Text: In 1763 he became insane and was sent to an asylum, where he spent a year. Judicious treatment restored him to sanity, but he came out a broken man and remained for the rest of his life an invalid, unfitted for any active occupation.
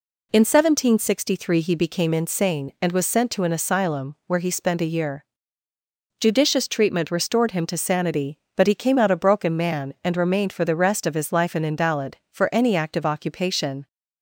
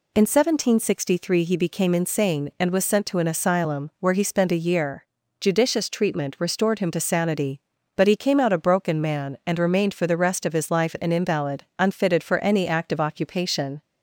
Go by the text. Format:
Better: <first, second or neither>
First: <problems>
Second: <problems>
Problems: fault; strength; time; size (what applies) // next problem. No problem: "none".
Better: second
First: skips "unfitted"; at 12.2 s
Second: none